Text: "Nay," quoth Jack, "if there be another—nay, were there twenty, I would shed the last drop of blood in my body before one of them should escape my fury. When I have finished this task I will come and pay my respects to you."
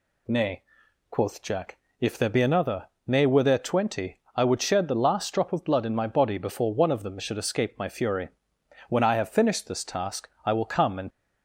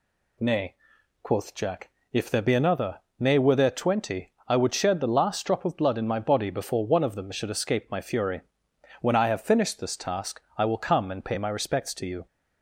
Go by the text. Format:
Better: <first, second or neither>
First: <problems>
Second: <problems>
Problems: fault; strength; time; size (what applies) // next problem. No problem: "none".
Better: second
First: pauses between "task" and "I"; slight; at 10.2 s; 0.16 s long // stops before "pay my respects to you"; at 11.1 s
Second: pauses between "task" and "I"; slight; at 10.3 s; 0.16 s long